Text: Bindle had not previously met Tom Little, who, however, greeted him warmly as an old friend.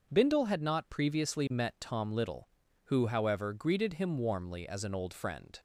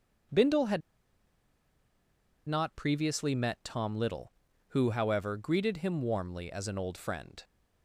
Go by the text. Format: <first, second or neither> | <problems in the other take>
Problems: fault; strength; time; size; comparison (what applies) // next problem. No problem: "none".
first | starts louder than the rest; until 2.9 s; 6.5 dB; also in the first // pauses between "had" and "not"; strong; at 0.8 s; 1.6 s long